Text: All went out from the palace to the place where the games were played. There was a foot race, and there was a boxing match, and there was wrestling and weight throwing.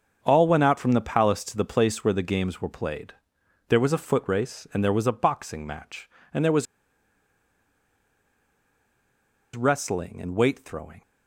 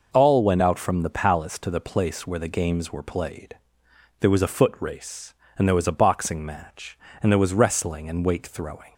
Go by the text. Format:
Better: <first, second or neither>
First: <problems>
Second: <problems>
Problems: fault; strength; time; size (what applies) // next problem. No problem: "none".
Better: second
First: starts louder than the rest; until 1.2 s; 6.5 dB // pauses between "was" and "wrestling"; strong; at 6.6 s; 2.9 s long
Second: none